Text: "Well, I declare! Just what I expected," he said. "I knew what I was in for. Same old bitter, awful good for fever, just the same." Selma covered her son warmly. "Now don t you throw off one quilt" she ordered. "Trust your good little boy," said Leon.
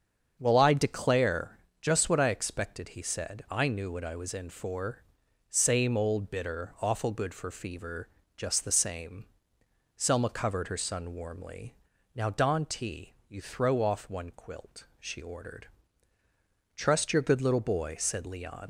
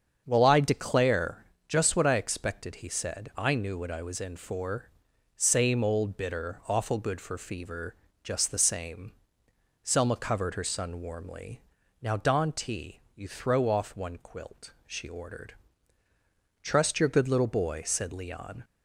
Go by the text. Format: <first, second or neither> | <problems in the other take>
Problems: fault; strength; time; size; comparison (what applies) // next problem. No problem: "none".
second | starts louder than the rest; strong; until 1.4 s; 7.5 dB; strong in the second // leaves "Leon" unfinished; at 18.6 s; 75 ms